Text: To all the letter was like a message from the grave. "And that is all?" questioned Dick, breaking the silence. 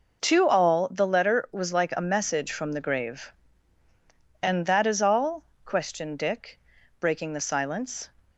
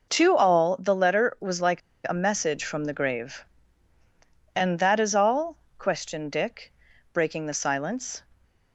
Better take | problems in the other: first | pauses between "like" and "a"; slight; at 1.8 s; 0.27 s long

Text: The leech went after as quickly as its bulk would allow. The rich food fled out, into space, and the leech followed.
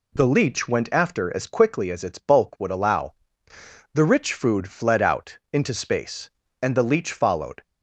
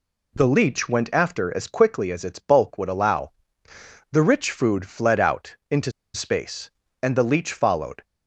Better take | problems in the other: first | pauses between "into" and "space"; slight; at 5.9 s; 0.23 s long

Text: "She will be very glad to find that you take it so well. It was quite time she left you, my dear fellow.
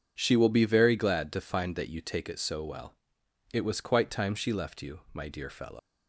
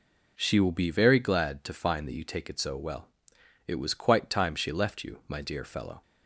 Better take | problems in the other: second | leaves "fellow" unfinished; at 5.7 s; 95 ms

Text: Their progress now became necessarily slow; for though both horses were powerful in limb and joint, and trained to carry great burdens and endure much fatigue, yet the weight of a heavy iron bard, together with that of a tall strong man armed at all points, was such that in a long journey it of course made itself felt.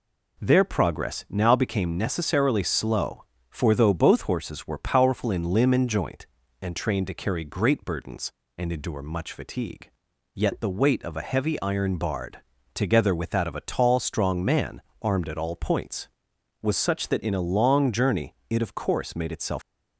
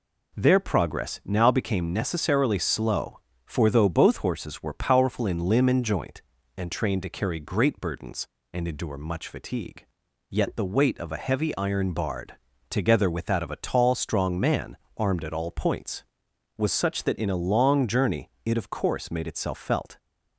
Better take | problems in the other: second | pauses between "man" and "armed"; slight; at 14.8 s; 0.22 s long; slight in the second // stops before "felt"; at 19.6 s

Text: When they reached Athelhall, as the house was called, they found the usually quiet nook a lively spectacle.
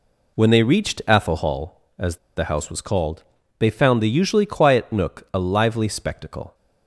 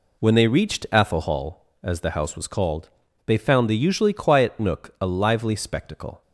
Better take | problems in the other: second | pauses between "as" and "the"; slight; at 2.1 s; 0.21 s long

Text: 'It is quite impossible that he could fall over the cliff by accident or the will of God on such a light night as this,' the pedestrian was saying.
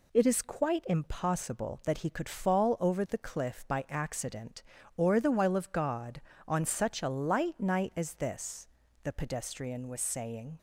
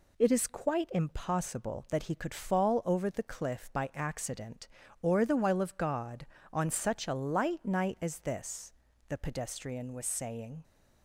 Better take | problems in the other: neither | none

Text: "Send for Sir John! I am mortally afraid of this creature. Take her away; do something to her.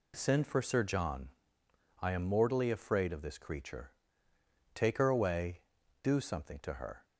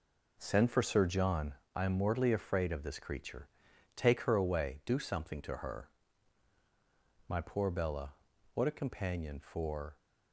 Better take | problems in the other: first | goes on to say "My poor Bella what a companion for"; strong; from 7.2 s on; 2.7 s long

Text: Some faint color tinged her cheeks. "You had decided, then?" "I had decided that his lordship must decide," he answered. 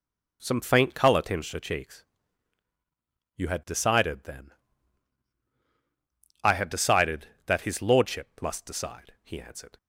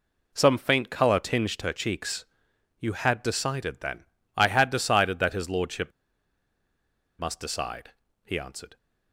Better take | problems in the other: first | pauses between "lordship" and "must"; strong; at 5.9 s; 1.2 s long

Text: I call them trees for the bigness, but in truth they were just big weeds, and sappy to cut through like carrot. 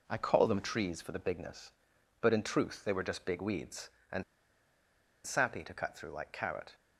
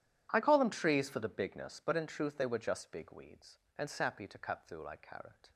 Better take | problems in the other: second | pauses between "and" and "sappy"; at 4.2 s; 1.0 s long

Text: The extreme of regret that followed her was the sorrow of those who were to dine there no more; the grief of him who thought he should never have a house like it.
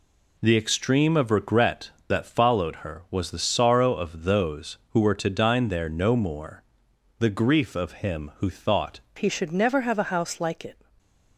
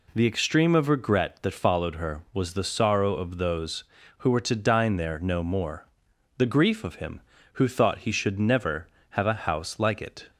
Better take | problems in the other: second | changes voice at "he"; from 9.1 s on; 1.6 s long

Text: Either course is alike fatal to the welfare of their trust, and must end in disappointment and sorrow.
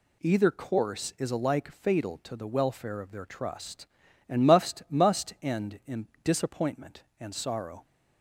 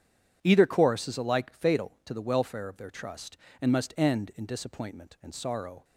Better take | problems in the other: second | says "must" twice; at 4.9 s // pauses between "in" and "disappointment"; slight; at 6.0 s; 0.18 s long

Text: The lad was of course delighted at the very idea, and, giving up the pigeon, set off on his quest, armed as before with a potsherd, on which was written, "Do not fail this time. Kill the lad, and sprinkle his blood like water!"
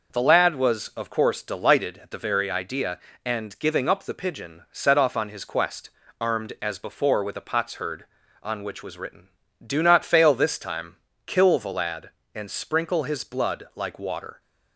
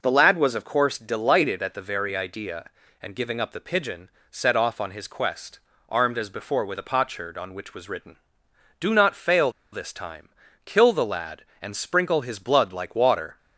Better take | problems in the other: first | pauses between "fail" and "this"; slight; at 9.5 s; 0.21 s long

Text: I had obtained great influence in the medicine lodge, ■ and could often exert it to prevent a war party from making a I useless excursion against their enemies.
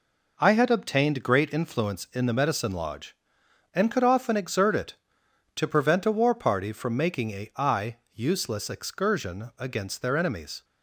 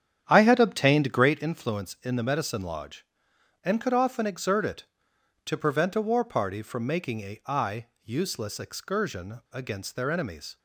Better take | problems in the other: first | starts louder than the rest; strong; until 1.5 s; 9 dB // pauses between "I" and "useless"; slight; at 7.8 s; 0.16 s long; slight in the first

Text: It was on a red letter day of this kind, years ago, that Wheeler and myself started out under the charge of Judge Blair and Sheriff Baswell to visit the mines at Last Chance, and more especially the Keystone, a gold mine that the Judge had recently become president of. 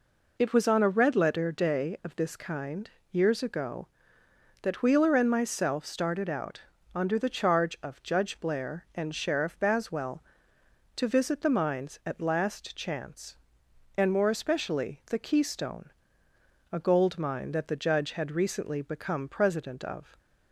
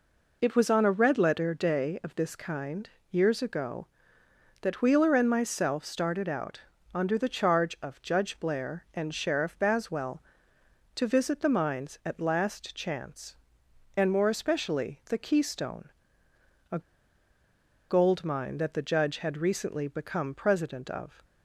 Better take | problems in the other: first | pauses between "out" and "under"; slight; at 6.6 s; 0.32 s long; slight in the first // pauses between "a" and "gold"; at 16.7 s; 1.0 s long

